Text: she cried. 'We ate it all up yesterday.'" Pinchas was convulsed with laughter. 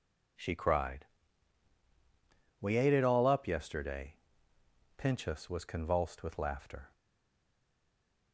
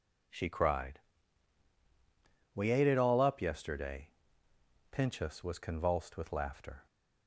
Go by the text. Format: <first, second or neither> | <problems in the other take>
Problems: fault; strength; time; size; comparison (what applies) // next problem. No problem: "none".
second | stays silent after the last word; noticeable; from 6.9 s on; 1.4 s long